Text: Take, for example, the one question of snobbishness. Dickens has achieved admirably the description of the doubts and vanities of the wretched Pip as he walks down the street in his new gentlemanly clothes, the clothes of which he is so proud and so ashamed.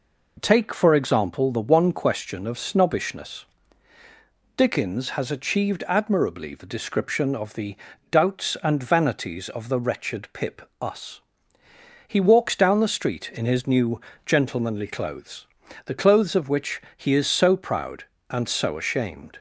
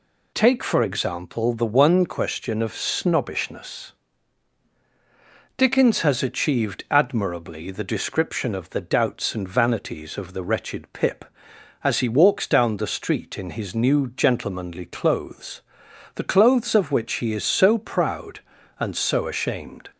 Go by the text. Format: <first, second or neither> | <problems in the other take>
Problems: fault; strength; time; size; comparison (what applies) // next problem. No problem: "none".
second | pauses between "the" and "doubts"; slight; at 7.7 s; 0.34 s long // says "us" for "as"; at 10.8 s // pauses between "new" and "gentlemanly"; slight; at 14.0 s; 0.24 s long // pauses between "which" and "he"; slight; at 16.8 s; 0.16 s long